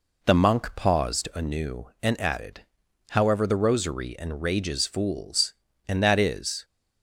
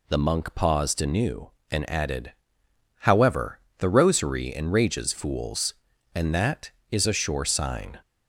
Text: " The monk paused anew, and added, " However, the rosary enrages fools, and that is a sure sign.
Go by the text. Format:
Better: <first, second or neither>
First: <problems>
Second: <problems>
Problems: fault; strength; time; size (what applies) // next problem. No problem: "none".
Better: second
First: stops before "a sure sign"; at 6.6 s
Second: none